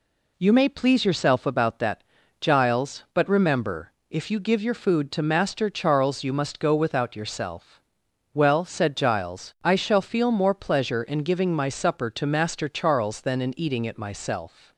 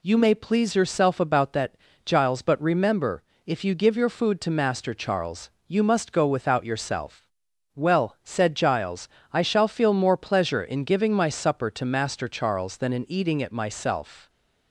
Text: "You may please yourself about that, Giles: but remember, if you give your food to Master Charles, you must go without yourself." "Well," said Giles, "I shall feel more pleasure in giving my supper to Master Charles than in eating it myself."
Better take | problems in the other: neither | none

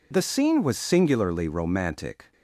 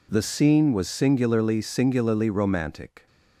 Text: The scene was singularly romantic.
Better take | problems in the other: first | says "singularly" twice; at 1.6 s

